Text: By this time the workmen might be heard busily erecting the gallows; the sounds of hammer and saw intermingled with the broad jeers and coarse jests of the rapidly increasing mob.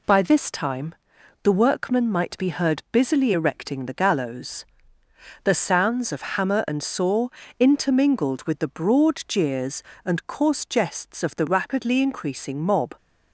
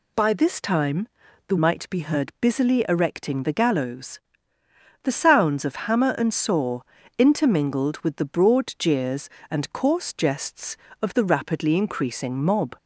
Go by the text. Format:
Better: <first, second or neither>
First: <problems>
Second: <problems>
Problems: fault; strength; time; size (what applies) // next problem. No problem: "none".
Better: first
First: pauses between "time" and "the"; noticeable; at 0.9 s; 0.50 s long // pauses between "saw" and "intermingled"; slight; at 7.2 s; 0.30 s long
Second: pauses between "time" and "the"; at 1.0 s; 0.40 s long // skips "workmen"; at 1.5 s // pauses between "saw" and "intermingled"; slight; at 6.8 s; 0.36 s long